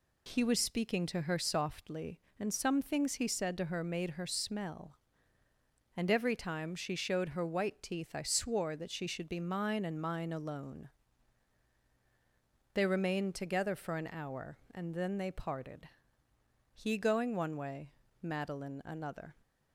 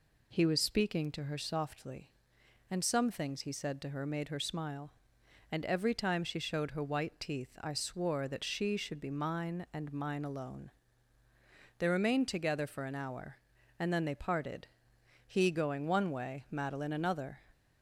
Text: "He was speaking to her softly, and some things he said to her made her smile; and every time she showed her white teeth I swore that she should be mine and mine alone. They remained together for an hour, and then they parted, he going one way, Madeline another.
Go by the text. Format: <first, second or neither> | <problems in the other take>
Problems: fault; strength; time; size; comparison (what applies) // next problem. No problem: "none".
second | says "smell" for "smile"; at 4.2 s